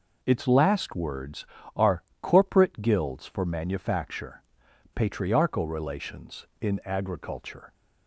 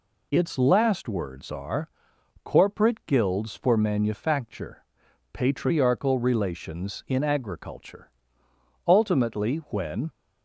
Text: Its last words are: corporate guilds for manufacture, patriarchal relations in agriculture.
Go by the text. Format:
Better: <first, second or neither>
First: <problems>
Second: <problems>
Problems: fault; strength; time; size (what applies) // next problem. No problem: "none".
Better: first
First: none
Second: goes on to say "Ultimately when"; noticeable; from 8.8 s on; 1.2 s long